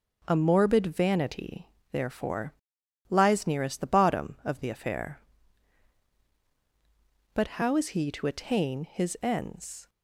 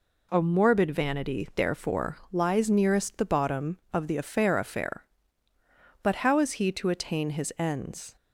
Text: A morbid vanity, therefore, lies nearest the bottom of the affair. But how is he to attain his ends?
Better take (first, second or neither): first